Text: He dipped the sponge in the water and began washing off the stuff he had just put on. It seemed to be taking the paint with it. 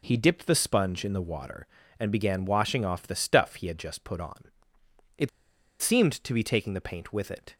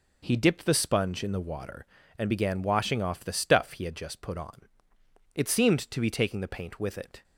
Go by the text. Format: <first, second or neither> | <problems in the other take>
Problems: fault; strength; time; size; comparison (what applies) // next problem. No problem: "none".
second | pauses between "It" and "seemed"; noticeable; at 5.2 s; 0.52 s long